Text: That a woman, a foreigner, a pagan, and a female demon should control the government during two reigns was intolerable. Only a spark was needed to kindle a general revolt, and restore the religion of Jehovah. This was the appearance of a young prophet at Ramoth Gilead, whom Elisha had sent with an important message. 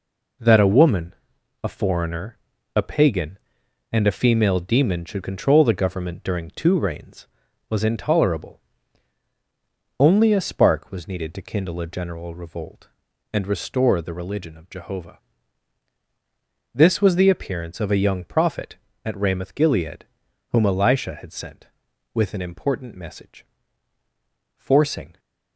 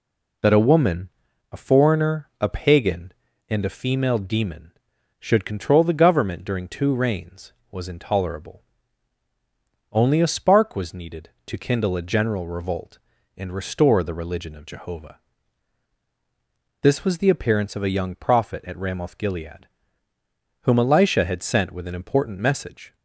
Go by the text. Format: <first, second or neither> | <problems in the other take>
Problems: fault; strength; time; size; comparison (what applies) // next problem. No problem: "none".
second | goes on to say "Forcing"; noticeable; from 24.5 s on; 0.62 s long